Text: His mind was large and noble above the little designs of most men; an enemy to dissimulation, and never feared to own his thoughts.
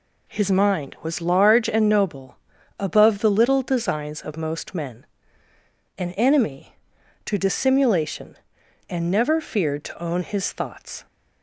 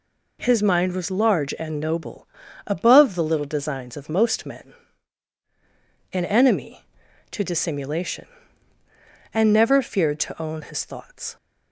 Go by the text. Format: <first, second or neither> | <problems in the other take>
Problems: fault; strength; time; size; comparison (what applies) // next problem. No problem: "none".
neither | pauses between "noble" and "above"; the same in both